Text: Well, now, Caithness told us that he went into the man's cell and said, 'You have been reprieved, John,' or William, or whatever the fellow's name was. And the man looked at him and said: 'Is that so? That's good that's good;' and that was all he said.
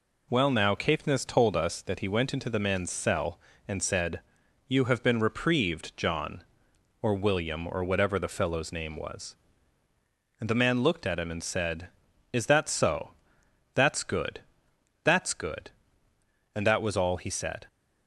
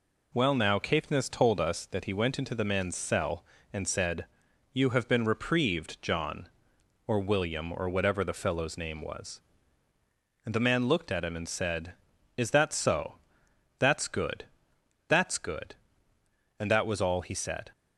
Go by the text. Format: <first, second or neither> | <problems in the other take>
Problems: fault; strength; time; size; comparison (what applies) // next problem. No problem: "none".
neither | pauses between "good" and "that's"; noticeable; the same in both